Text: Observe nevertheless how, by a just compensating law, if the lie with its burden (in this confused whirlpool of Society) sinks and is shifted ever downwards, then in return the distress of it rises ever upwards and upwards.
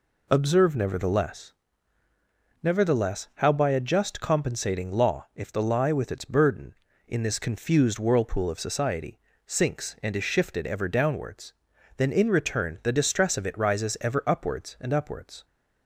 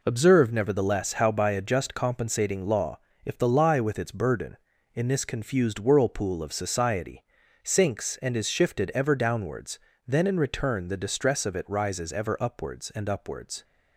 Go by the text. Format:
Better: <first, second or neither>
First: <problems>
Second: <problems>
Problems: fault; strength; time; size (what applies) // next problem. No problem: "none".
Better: second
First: says "nevertheless" twice; at 2.6 s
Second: none